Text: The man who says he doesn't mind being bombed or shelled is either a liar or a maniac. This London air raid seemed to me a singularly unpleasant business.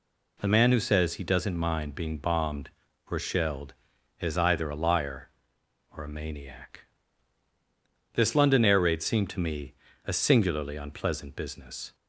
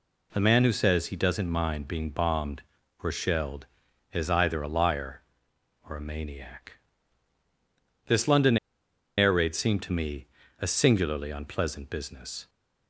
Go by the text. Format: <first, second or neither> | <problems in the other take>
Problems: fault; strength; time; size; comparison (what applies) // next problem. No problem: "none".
first | pauses between "London" and "air"; noticeable; at 8.5 s; 0.61 s long // pauses between "me" and "a"; slight; at 10.2 s; 0.34 s long; slight in the first